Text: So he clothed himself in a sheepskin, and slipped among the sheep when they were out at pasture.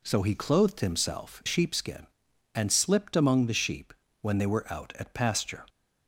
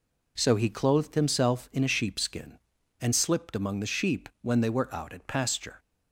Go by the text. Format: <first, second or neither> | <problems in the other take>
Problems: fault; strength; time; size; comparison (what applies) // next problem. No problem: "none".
second | skips "in a"; at 1.4 s // pauses between "sheep" and "when"; slight; at 3.9 s; 0.30 s long